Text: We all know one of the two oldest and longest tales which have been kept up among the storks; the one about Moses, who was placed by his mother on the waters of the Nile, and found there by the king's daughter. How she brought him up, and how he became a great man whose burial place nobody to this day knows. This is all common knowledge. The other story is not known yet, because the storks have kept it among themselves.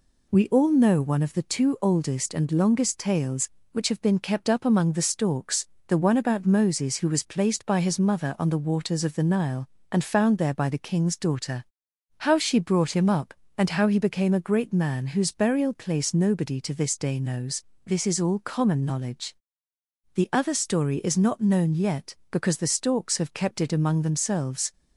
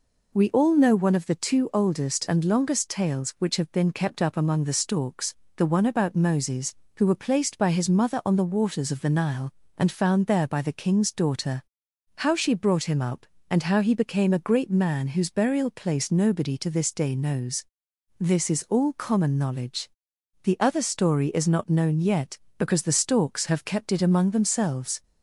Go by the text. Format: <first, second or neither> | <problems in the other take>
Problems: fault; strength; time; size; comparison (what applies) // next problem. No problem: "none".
first | says "were" for "was"; at 7.0 s